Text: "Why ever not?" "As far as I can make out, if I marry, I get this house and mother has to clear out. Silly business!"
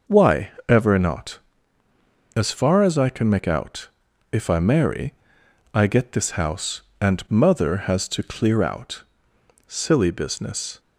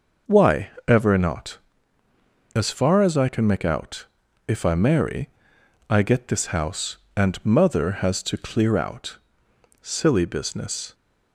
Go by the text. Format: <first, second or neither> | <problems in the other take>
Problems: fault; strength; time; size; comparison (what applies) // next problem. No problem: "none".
neither | pauses between "Why" and "ever"; slight; the same in both